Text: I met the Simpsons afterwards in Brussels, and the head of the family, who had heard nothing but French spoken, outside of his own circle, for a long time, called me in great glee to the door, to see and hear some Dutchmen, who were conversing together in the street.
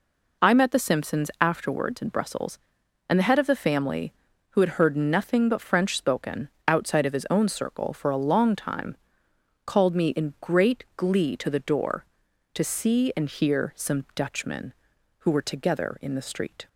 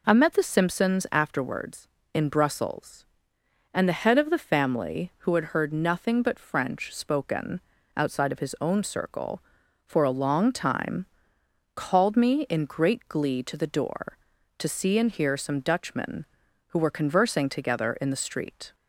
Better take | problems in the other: second | skips "conversing"; at 15.4 s

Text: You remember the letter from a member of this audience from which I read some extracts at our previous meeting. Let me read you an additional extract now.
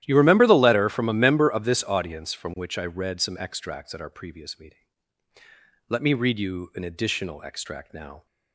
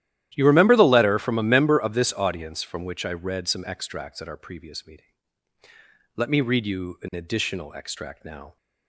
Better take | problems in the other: neither | starts louder than the rest; strong; the same in both

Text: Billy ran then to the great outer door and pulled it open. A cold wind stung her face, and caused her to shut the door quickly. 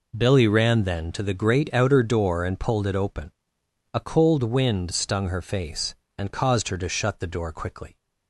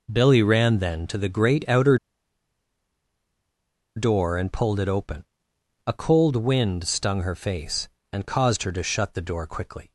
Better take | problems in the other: first | pauses between "outer" and "door"; strong; at 1.9 s; 1.9 s long

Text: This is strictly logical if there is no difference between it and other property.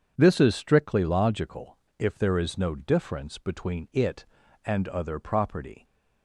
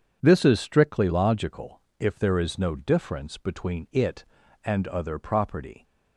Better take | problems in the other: neither | pauses between "logical" and "if"; slight; the same in both

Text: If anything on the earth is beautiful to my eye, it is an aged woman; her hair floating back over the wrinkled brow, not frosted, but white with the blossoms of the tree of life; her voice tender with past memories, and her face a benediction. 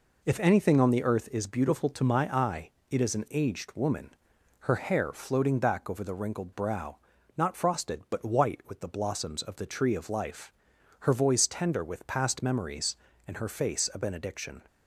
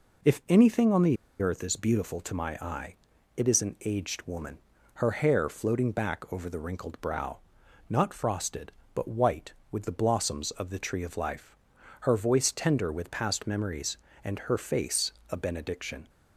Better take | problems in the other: first | pauses between "the" and "earth"; slight; at 1.1 s; 0.24 s long // pauses between "face" and "a"; slight; at 15.1 s; 0.18 s long

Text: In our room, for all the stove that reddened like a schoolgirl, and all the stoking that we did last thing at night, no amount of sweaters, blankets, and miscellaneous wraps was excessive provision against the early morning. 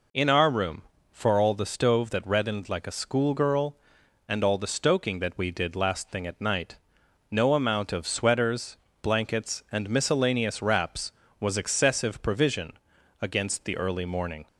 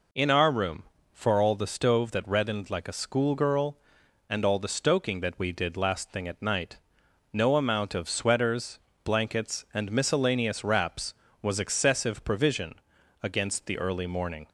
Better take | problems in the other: neither | pauses between "provision" and "against"; noticeable; the same in both

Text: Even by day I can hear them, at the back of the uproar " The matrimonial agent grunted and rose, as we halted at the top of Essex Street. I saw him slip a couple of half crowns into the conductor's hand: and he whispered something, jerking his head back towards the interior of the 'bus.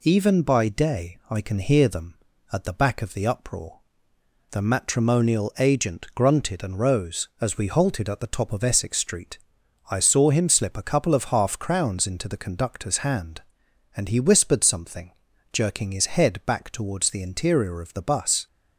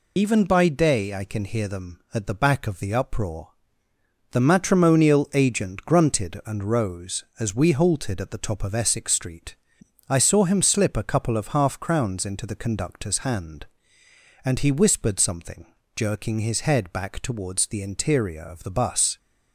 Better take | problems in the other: first | loses the start of "Even"; at 0.1 s; 70 ms

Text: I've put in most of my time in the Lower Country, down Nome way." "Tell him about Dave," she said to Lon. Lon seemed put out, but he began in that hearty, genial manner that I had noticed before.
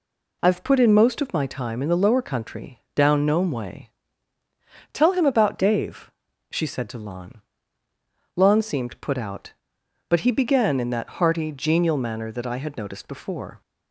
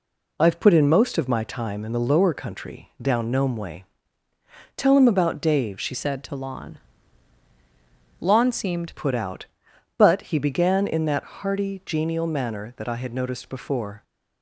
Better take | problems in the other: first | changes voice from "said" to "seemed"; from 5.9 to 8.9 s; 3.0 s long

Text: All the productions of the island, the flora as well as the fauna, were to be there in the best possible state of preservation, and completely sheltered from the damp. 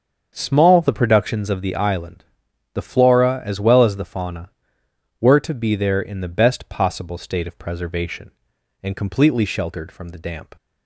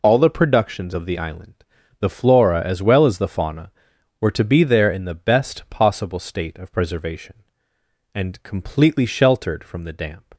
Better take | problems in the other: second | starts louder than the rest; until 1.3 s; 7 dB // says "Small" for "All"; at 0.3 s

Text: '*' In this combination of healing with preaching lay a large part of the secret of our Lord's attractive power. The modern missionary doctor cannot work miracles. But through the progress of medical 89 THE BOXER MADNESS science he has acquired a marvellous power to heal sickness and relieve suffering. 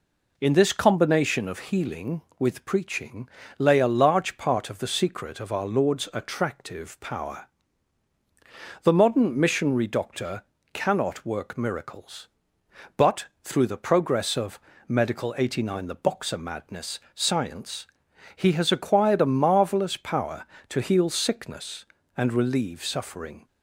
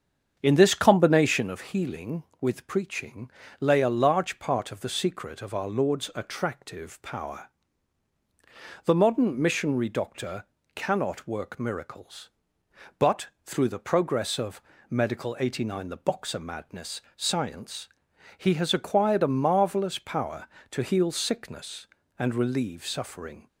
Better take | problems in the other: first | starts louder than the rest; strong; until 1.5 s; 7.5 dB // pauses between "preaching" and "lay"; slight; at 3.2 s; 0.32 s long; slight in the first // pauses between "doctor" and "cannot"; slight; at 10.4 s; 0.32 s long; slight in the first // pauses between "But" and "through"; slight; at 13.2 s; 0.16 s long; slight in the first // pauses between "of" and "medical"; slight; at 14.6 s; 0.26 s long; slight in the first // pauses between "science" and "he"; noticeable; at 17.8 s; 0.50 s long; noticeable in the first

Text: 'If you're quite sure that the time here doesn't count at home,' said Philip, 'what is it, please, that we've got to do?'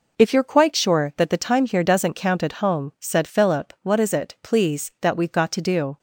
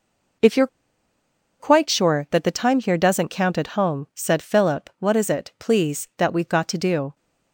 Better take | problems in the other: first | pauses between "you're" and "quite"; noticeable; at 0.6 s; 0.93 s long

